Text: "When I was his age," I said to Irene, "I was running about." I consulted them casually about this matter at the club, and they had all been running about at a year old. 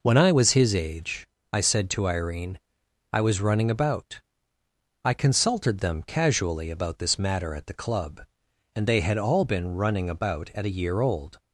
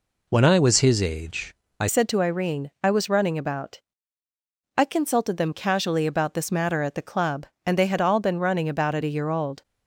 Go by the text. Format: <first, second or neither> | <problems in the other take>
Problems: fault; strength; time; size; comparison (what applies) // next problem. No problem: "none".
first | changes voice at "said"; from 1.8 s on; 7.8 s long